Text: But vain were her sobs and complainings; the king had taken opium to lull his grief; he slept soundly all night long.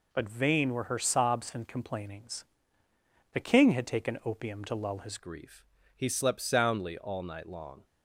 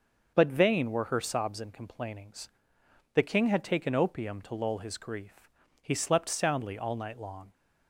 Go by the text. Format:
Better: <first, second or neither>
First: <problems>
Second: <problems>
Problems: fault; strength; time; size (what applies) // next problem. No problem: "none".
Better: second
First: changes voice at "grief"; from 5.1 s on; 2.7 s long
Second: none